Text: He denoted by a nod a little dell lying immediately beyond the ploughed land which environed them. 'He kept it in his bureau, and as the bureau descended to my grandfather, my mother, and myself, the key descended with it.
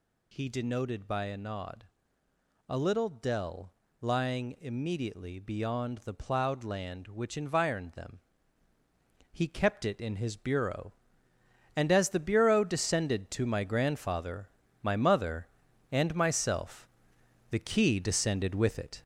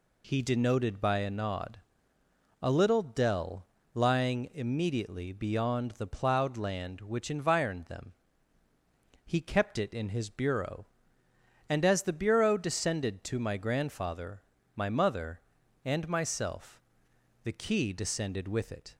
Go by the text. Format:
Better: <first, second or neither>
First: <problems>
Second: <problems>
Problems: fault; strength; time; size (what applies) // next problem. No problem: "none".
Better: second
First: gets louder; noticeable; throughout; 5.5 dB // pauses between "nod" and "a"; noticeable; at 1.8 s; 0.82 s long // pauses between "dell" and "lying"; slight; at 3.7 s; 0.26 s long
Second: pauses between "nod" and "a"; noticeable; at 1.7 s; 0.82 s long // pauses between "dell" and "lying"; slight; at 3.6 s; 0.26 s long